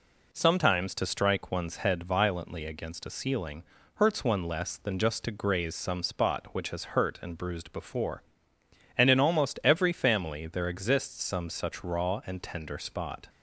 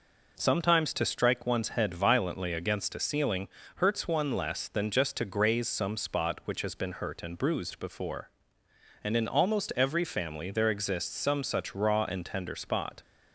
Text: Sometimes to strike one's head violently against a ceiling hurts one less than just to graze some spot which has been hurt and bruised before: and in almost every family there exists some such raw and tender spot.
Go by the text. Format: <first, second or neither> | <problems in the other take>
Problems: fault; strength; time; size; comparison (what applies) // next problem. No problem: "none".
second | pauses between "ceiling" and "hurts"; slight; at 3.6 s; 0.32 s long; slight in the second // skips "been"; at 6.9 s